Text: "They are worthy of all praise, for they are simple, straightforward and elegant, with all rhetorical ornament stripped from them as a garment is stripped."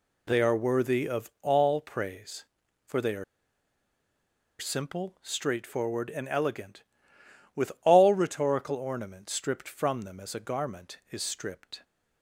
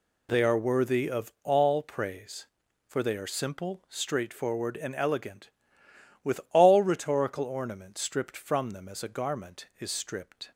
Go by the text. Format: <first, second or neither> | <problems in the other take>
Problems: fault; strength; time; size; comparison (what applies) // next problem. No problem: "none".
second | pauses between "are" and "simple"; strong; at 3.2 s; 1.3 s long